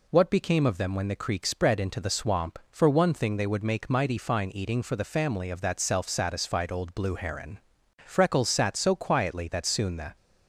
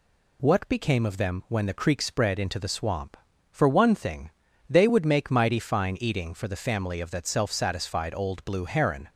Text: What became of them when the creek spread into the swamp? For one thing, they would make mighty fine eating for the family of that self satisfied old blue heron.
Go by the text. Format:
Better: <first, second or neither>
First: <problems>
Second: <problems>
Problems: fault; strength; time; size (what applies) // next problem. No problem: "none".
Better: second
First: goes on to say "Freckles sat so quietly that soon the"; strong; from 8.0 s on; 2.1 s long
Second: none